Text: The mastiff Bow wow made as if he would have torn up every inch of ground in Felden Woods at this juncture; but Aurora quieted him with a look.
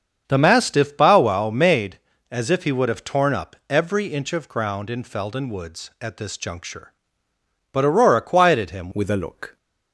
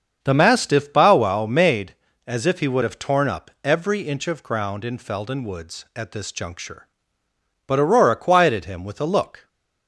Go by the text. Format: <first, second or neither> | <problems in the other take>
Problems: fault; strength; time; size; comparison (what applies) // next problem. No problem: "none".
second | starts louder than the rest; until 1.2 s; 7 dB; also in the second // changes voice at "with"; from 8.9 s on; 0.6 s long